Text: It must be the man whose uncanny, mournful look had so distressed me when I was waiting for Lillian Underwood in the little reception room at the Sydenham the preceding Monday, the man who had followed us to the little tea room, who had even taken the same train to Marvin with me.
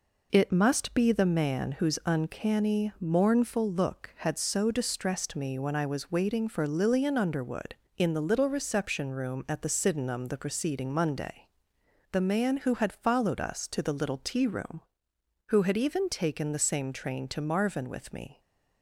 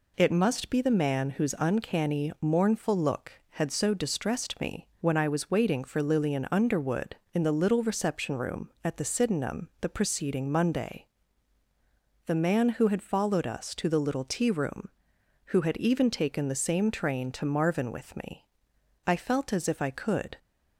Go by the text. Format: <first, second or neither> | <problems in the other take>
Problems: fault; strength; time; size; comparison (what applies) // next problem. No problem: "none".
first | goes on to say "I felt as if I could"; noticeable; from 19.0 s on; 1.3 s long